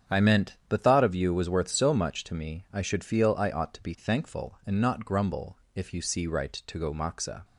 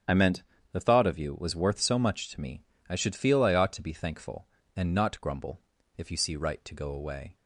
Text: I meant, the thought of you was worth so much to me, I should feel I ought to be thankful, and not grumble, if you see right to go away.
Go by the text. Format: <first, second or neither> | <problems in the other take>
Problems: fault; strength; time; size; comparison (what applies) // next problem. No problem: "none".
second | starts louder than the rest; strong; until 1.2 s; 8.5 dB; strong in the second // says "moxa" for "away"; at 6.9 s